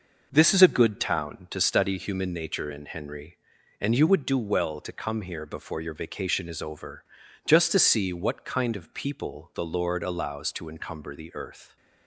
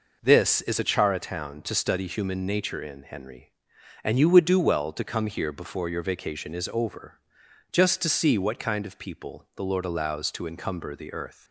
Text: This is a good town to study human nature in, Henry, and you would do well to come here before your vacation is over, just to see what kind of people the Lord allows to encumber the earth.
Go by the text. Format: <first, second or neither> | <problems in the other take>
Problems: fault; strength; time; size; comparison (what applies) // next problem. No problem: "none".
first | says "chara" for "good"; at 0.8 s